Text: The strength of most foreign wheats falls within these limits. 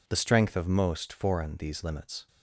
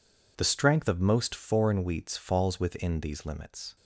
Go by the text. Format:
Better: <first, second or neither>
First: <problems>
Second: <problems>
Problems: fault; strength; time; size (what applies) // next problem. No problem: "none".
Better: second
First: skips "wheats falls within"; at 1.5 s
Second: none